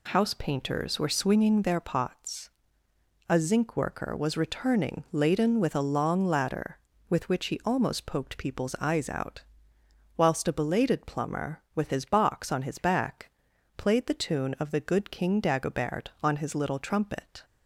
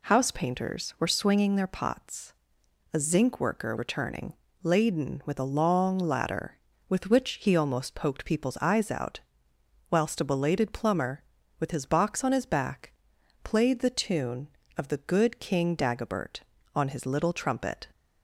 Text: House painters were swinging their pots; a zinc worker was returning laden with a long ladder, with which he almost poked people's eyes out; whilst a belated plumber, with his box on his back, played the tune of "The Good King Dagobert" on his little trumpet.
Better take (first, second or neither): first